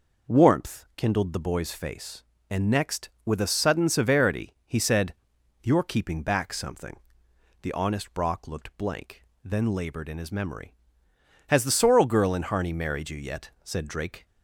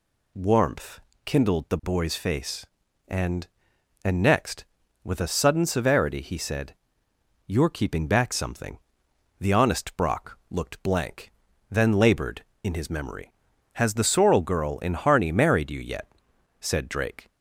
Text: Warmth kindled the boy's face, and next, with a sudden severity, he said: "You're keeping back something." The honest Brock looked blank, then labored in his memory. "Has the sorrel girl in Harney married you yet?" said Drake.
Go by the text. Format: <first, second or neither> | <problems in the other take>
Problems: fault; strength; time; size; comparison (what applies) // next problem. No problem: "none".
first | pauses between "Warmth" and "kindled"; slight; at 1.0 s; 0.24 s long // says "and" twice; at 4.0 s